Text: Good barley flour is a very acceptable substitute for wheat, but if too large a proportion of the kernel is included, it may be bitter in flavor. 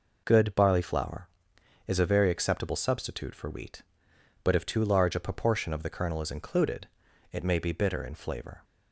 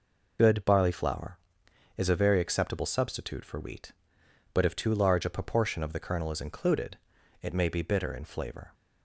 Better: first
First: none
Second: loses the start of "Good"; at 0.3 s; 40 ms

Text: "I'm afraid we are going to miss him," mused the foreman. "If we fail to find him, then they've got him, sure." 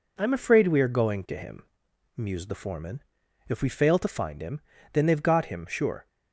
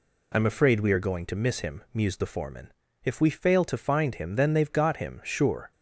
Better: second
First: skips "miss"; at 1.3 s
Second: none

